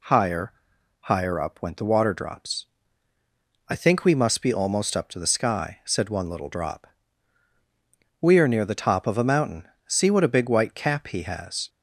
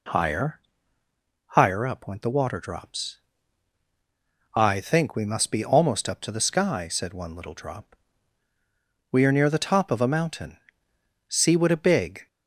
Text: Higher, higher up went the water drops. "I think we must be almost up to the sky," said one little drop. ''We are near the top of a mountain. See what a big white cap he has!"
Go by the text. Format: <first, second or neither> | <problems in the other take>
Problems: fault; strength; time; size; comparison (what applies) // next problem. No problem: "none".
first | stops before "white cap he has"; at 12.2 s